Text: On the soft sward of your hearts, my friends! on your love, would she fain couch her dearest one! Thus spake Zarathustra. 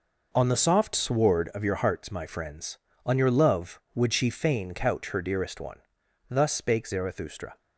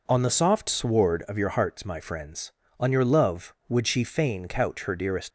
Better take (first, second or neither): first